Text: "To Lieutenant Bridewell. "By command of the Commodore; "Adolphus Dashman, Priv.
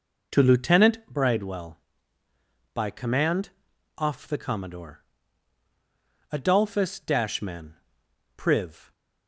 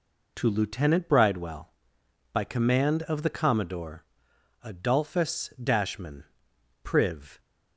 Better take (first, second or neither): second